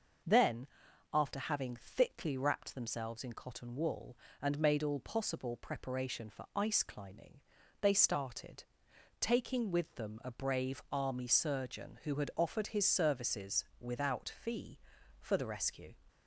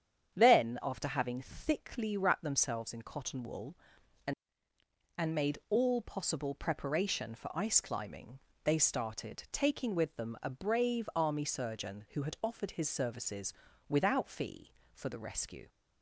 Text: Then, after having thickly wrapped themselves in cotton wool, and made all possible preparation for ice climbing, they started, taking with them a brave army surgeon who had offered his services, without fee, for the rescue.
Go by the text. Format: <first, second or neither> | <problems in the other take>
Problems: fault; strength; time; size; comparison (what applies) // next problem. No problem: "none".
first | starts louder than the rest; strong; until 1.3 s; 8.5 dB // says "and" twice; at 5.1 s